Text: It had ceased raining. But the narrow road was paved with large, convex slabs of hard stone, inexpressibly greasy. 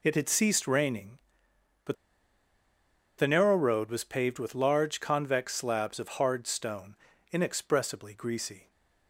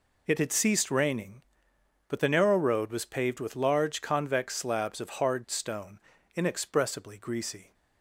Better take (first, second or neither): second